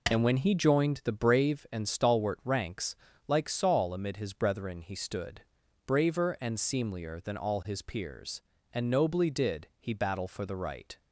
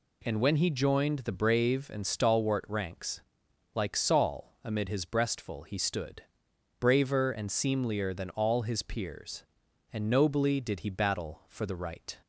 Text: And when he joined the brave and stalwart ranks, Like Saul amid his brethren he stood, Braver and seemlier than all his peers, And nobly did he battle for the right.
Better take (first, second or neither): first